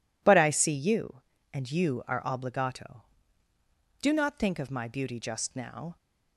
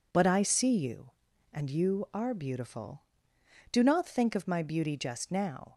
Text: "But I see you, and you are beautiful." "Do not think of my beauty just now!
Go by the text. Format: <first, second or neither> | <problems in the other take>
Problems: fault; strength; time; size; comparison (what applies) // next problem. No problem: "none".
second | says "obligato" for "beautiful"; at 2.2 s